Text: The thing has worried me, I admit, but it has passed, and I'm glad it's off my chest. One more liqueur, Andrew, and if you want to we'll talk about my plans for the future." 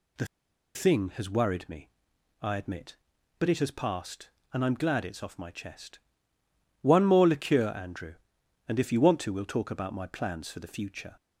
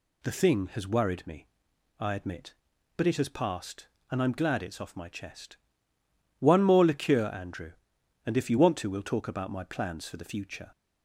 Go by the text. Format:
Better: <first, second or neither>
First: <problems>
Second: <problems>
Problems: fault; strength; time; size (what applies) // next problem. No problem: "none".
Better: second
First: pauses between "The" and "thing"; noticeable; at 0.2 s; 0.49 s long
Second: none